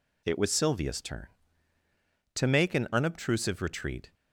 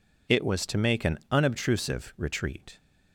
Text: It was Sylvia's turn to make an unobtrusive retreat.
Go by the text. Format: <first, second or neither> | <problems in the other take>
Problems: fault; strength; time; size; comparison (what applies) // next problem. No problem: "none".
first | skips "Sylvia's turn"; at 0.6 s